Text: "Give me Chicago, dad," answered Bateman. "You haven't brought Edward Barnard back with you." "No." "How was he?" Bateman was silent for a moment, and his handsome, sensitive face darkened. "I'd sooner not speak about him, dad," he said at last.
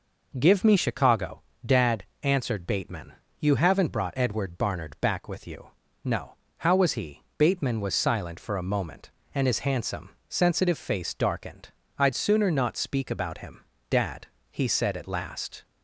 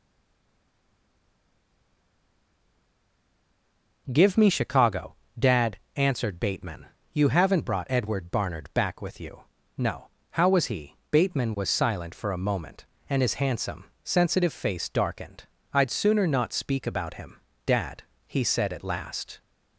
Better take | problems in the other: first | stays silent before the first word; strong; until 4.0 s; 4.0 s long

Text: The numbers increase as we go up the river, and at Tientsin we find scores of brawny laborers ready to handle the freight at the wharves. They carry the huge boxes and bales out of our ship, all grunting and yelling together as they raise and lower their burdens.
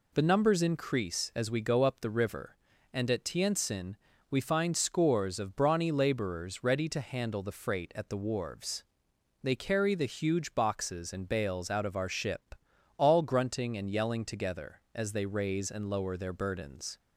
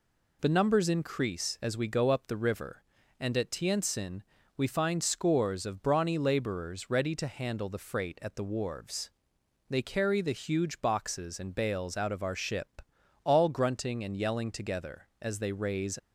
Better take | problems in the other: first | pauses between "Tientsin" and "we"; slight; at 4.2 s; 0.34 s long; slight in the first // stops before "and lower their burdens"; at 15.9 s

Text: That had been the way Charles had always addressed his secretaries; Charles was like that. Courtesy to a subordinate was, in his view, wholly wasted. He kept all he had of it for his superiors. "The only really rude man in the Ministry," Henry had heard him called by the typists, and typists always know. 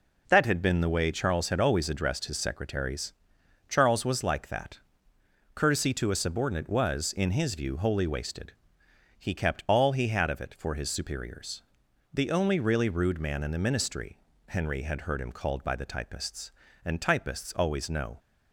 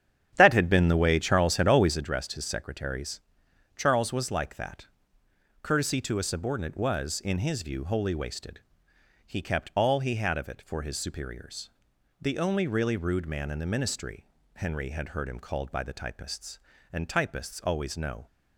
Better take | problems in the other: first | starts louder than the rest; strong; until 2.0 s; 9.5 dB

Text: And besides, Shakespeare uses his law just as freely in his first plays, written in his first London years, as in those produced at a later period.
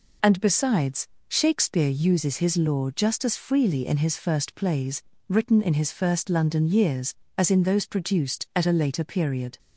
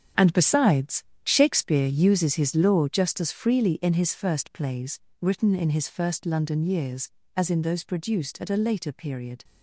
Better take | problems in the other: first | gets quieter; strong; throughout; 10.5 dB

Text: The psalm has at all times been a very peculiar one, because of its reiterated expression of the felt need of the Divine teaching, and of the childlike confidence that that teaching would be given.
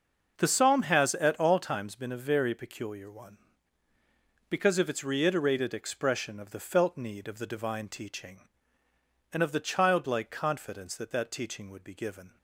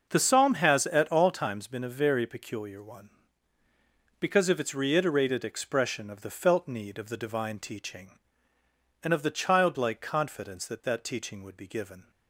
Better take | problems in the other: neither | starts louder than the rest; noticeable; the same in both

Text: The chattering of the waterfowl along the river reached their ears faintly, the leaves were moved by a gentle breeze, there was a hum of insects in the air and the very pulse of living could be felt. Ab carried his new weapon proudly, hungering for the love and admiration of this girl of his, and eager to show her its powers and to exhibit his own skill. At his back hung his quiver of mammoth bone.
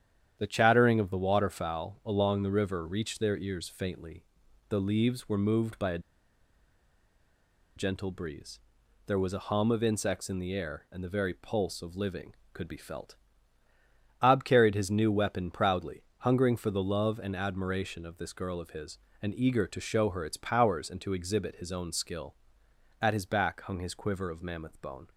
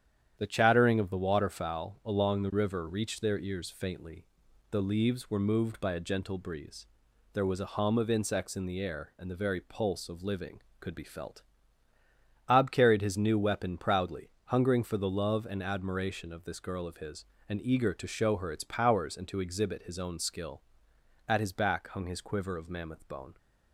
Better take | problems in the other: second | starts louder than the rest; strong; until 1.4 s; 9.5 dB; strong in the second // pauses between "a" and "gentle"; strong; at 5.9 s; 1.7 s long

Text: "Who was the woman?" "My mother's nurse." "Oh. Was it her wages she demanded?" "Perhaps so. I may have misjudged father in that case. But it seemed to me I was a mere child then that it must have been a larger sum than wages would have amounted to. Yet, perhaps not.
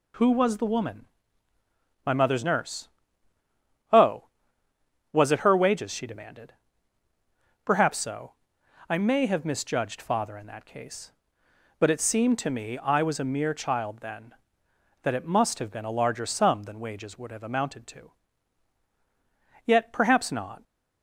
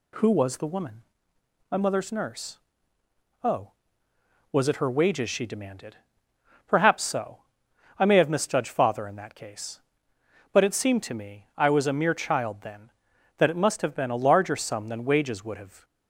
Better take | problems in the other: first | stops before "amounted to Yet perhaps not"; at 15.8 s

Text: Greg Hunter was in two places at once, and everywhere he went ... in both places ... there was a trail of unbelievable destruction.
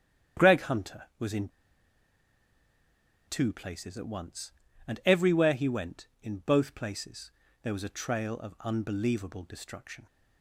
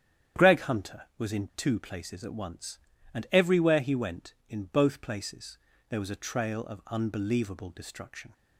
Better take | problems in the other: second | starts louder than the rest; strong; until 1.4 s; 9.5 dB; strong in the second // pauses between "in" and "two"; strong; at 1.4 s; 1.7 s long

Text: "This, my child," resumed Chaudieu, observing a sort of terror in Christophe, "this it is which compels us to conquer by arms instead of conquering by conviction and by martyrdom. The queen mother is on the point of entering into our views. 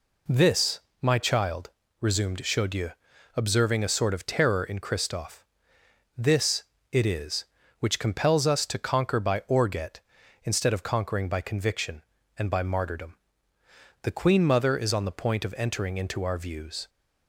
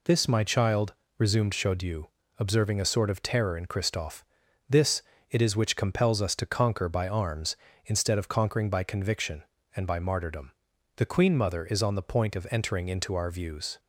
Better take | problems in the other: second | pauses between "this" and "it"; slight; at 6.6 s; 0.26 s long; slight in the second // says "orget" for "arms"; at 9.4 s

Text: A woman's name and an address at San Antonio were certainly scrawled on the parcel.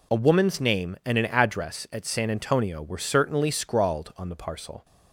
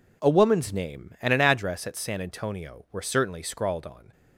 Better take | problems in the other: first | stops before "the parcel"; at 4.1 s

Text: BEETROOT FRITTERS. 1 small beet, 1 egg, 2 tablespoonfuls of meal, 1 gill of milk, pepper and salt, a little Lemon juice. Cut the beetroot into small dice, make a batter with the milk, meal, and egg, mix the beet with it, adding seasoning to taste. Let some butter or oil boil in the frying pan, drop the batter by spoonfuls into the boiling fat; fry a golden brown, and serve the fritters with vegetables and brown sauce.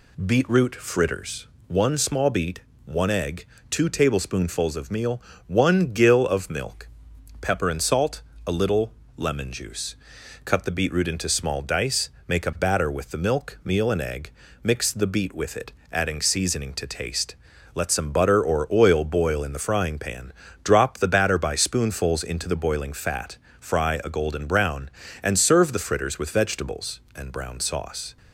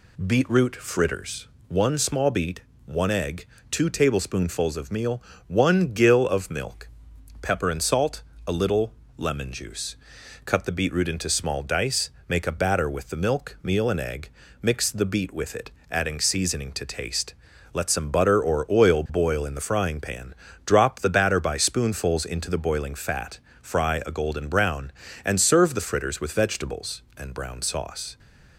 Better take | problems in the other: neither | pauses between "little" and "Lemon"; slight; the same in both

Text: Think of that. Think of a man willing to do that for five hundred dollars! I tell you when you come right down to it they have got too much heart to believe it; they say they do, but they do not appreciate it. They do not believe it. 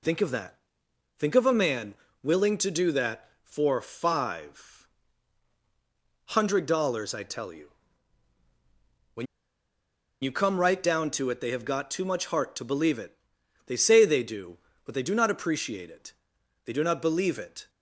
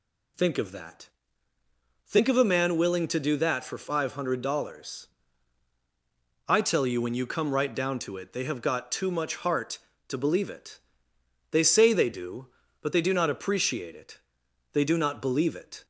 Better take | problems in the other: second | pauses between "man" and "willing"; slight; at 1.9 s; 0.28 s long // pauses between "five" and "hundred"; strong; at 4.8 s; 1.4 s long // pauses between "you" and "when"; strong; at 7.6 s; 1.4 s long // pauses between "when" and "you"; noticeable; at 9.2 s; 0.97 s long

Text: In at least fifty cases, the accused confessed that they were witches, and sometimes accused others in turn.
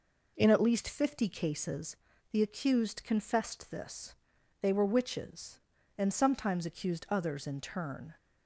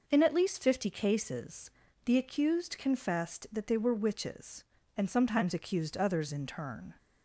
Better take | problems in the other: second | says "this" for "that"; at 3.7 s

